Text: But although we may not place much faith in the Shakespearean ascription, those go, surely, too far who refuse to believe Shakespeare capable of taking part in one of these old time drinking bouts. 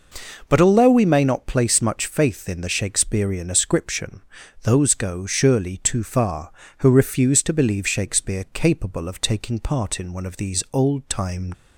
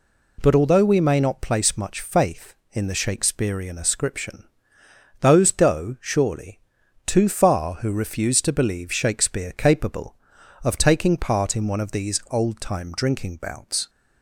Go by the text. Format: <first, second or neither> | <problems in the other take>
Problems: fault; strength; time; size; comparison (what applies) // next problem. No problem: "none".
second | stops before "drinking bouts"; at 11.5 s